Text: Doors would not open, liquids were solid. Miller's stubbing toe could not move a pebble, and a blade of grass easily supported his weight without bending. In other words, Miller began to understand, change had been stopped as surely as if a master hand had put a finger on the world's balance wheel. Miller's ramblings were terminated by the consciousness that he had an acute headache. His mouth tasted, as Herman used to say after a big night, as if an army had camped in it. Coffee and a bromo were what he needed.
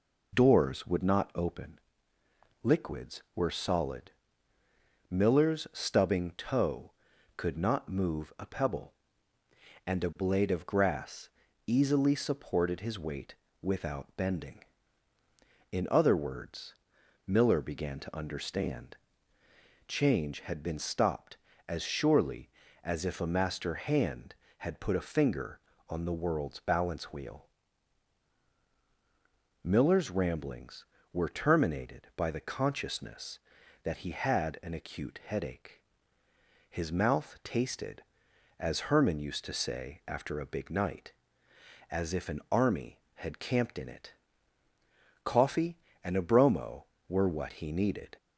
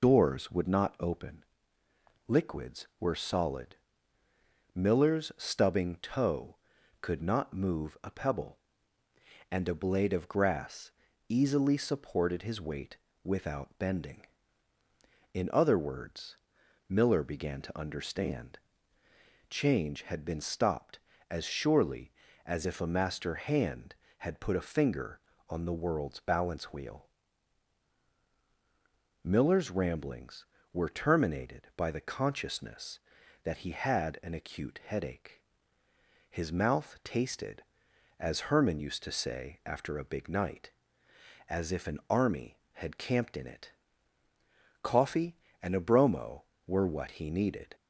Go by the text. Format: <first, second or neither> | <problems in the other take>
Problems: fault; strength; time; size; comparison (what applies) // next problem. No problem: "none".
first | loses the start of "Doors"; at 0.0 s; 50 ms // pauses between "grass" and "easily"; at 10.9 s; 0.38 s long; also in the first // pauses between "weight" and "without"; slight; at 12.9 s; 0.28 s long; slight in the first